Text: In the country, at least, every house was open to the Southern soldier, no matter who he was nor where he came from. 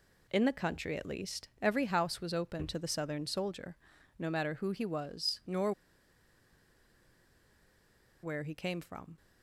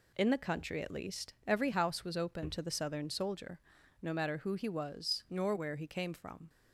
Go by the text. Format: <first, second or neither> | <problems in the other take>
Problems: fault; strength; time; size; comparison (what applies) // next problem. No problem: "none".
second | pauses between "nor" and "where"; strong; at 5.7 s; 2.5 s long